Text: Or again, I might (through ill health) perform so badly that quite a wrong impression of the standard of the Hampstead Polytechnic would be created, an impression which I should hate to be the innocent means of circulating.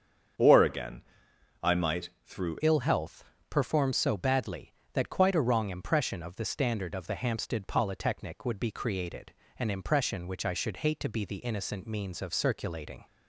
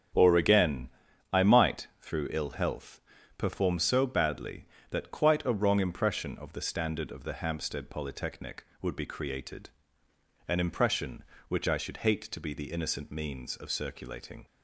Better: second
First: starts louder than the rest; strong; until 1.9 s; 7.5 dB // changes voice at "ill"; from 2.6 s on; 10.4 s long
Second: starts louder than the rest; strong; until 1.5 s; 8 dB

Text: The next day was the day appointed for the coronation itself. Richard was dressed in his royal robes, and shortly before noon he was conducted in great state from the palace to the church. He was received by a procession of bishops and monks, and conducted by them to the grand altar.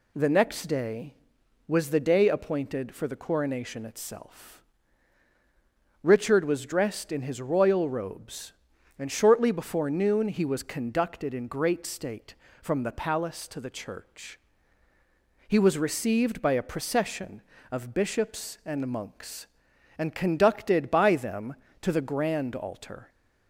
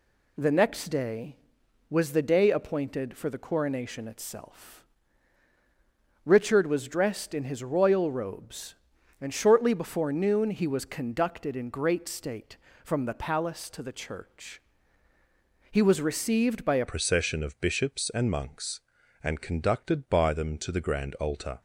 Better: first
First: none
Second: changes voice at "procession"; from 16.8 s on; 4.8 s long

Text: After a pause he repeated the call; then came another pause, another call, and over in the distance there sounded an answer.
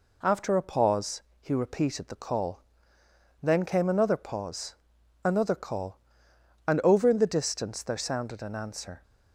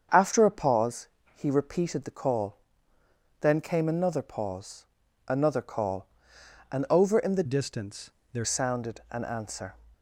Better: first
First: pauses between "pause" and "he"; slight; at 1.2 s; 0.18 s long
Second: starts louder than the rest; strong; until 1.4 s; 7 dB // pauses between "pause" and "he"; slight; at 1.0 s; 0.30 s long // changes voice from "distance" to "there"; from 7.4 to 8.4 s; 1.0 s long // pauses between "distance" and "there"; slight; at 8.0 s; 0.24 s long

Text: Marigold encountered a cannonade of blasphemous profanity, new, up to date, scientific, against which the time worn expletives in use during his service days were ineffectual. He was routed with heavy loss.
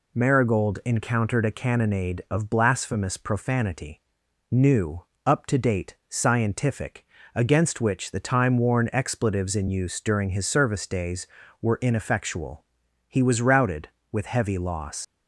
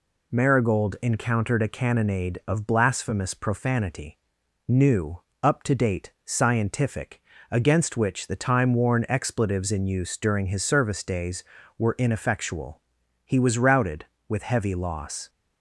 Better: second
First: leaves "loss" unfinished; at 15.0 s; 75 ms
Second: none

